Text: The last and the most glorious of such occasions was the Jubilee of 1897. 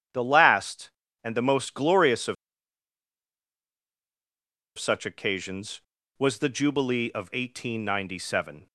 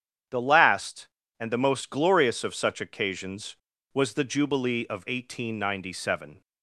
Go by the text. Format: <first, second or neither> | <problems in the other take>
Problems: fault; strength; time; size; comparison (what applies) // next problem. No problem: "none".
second | starts louder than the rest; strong; until 1.4 s; 9 dB; strong in the second // pauses between "of" and "such"; strong; at 2.3 s; 2.4 s long